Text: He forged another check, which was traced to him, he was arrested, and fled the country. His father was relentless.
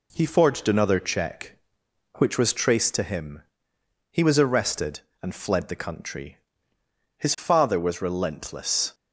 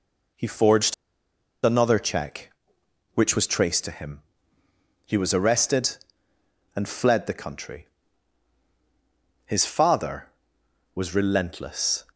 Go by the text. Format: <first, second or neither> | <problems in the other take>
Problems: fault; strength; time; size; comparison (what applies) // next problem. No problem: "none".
first | pauses between "forged" and "another"; noticeable; at 0.9 s; 0.70 s long